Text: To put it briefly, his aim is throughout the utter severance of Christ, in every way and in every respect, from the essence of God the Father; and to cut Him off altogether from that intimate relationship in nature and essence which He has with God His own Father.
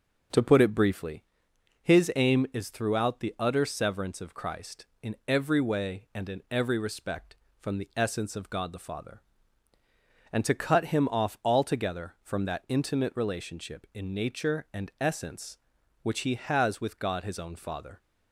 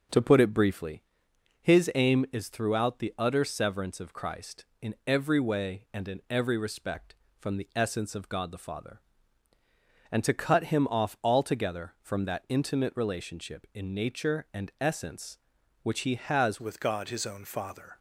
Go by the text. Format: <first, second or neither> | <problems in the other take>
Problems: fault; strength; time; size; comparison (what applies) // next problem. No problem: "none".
first | changes voice at "with"; from 16.6 s on; 1.3 s long